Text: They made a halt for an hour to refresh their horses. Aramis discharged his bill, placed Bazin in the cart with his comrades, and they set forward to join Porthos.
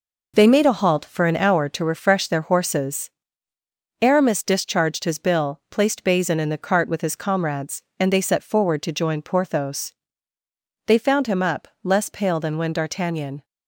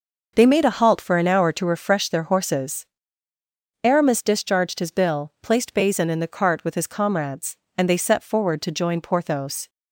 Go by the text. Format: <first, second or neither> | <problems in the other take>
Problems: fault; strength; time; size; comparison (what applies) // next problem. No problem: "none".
second | goes on to say "They found him up less pale than when D'Artagnan"; strong; from 10.8 s on; 2.5 s long